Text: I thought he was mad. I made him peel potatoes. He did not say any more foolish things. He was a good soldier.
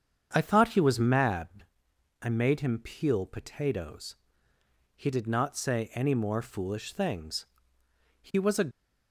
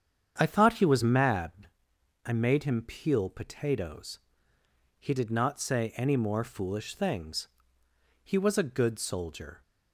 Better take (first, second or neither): second